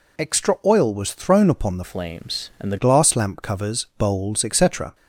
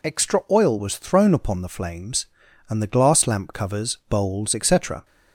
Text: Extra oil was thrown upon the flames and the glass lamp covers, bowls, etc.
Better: second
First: changes voice from "flames" to "the"; from 1.8 to 2.7 s; 0.9 s long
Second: none

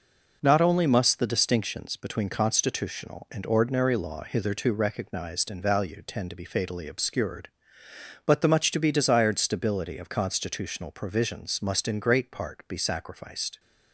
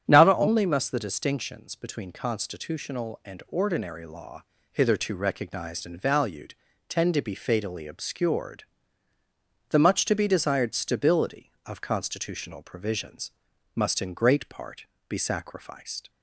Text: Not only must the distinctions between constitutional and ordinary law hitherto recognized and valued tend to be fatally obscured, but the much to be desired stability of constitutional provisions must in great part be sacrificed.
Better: first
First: none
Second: starts louder than the rest; strong; until 1.0 s; 9 dB // pauses between "law" and "hitherto"; slight; at 4.4 s; 0.28 s long // pauses between "valued" and "tend"; slight; at 6.5 s; 0.34 s long // skips "but"; at 9.1 s // pauses between "provisions" and "must"; at 13.3 s; 0.44 s long // pauses between "part" and "be"; slight; at 14.8 s; 0.22 s long

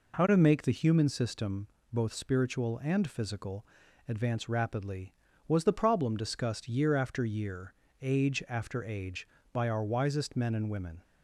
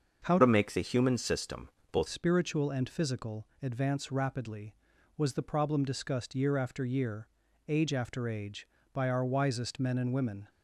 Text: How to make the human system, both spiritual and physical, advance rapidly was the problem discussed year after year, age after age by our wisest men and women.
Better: first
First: none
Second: starts louder than the rest; until 1.2 s; 7 dB // changes voice from "to" to "both"; from 0.3 to 2.0 s; 1.7 s long

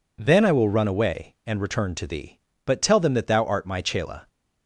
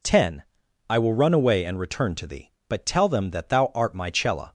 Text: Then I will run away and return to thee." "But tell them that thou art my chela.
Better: first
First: none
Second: says "Ten" for "Then"; at 0.0 s

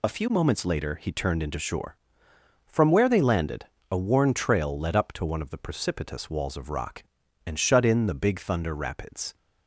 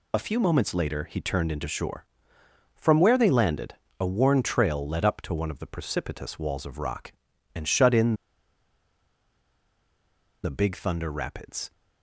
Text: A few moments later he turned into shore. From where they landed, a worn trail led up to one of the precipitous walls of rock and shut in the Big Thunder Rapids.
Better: first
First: none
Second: pauses between "in" and "the"; strong; at 8.1 s; 2.2 s long

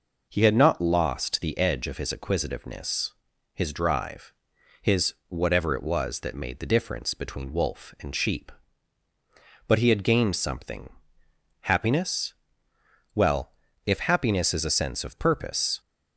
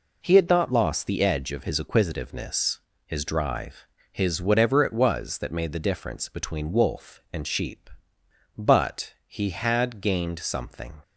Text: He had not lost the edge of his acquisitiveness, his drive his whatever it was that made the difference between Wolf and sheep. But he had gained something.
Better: second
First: pauses between "drive" and "his"; noticeable; at 4.3 s; 0.48 s long // goes on to say "Happiness Well if happiness is a sense of purpose"; strong; from 11.6 s on; 4.1 s long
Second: pauses between "drive" and "his"; slight; at 3.8 s; 0.28 s long

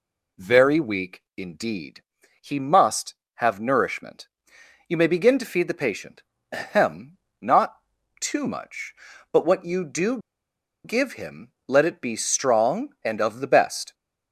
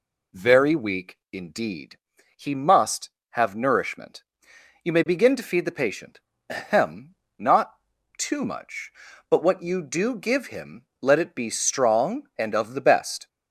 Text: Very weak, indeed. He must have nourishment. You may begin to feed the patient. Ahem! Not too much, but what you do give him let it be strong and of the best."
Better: second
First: pauses between "Not" and "too"; at 7.7 s; 0.44 s long // pauses between "do" and "give"; noticeable; at 10.1 s; 0.66 s long // pauses between "him" and "let"; slight; at 11.5 s; 0.16 s long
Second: pauses between "Not" and "too"; at 7.7 s; 0.44 s long // pauses between "him" and "let"; slight; at 10.8 s; 0.16 s long

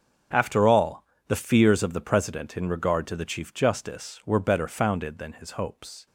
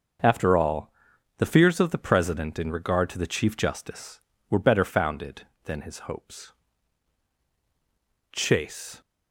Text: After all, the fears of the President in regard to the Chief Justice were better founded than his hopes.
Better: first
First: starts louder than the rest; until 1.5 s; 6.5 dB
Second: starts louder than the rest; until 1.6 s; 6.5 dB // goes on to say "Chase"; noticeable; from 8.3 s on; 0.68 s long

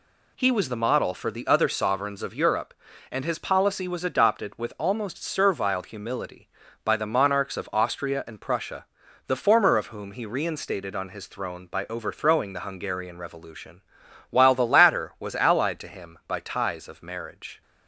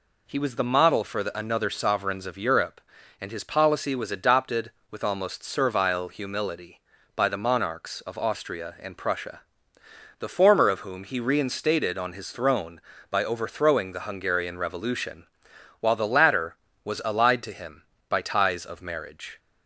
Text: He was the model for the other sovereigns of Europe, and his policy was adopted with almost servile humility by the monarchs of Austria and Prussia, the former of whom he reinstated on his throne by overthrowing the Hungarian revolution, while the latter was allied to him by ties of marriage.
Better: first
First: none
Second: says "another" for "other"; at 1.3 s

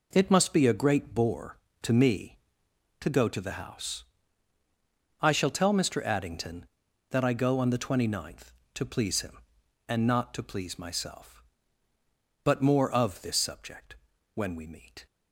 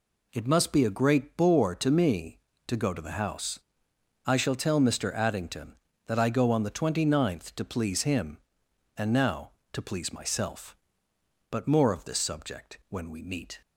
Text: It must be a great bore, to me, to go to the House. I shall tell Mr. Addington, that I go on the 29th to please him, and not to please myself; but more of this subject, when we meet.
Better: first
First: none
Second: says "now" for "not"; at 9.1 s

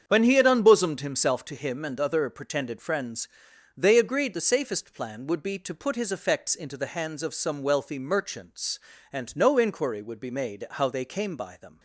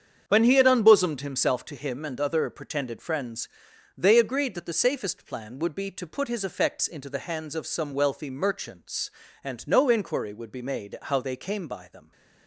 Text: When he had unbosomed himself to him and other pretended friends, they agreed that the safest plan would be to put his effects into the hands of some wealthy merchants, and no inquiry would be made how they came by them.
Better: second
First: starts louder than the rest; strong; until 1.0 s; 7.5 dB // skips "that"; at 4.3 s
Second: starts louder than the rest; strong; until 1.2 s; 7.5 dB

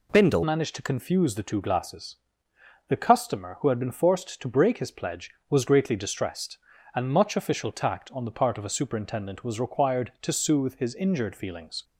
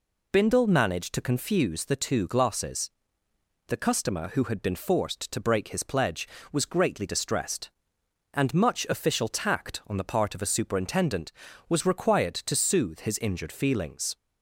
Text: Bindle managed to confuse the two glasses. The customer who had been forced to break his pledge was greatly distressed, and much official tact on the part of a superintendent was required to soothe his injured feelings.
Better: second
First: changes voice at "managed"; from 0.4 s on; 11.4 s long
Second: none

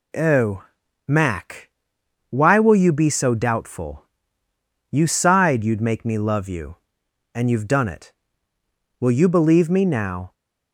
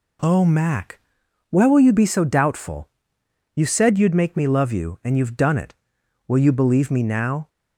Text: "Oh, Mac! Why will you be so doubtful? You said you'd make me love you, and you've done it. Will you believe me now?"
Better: second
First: says "sighed" for "said"; at 5.0 s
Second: none

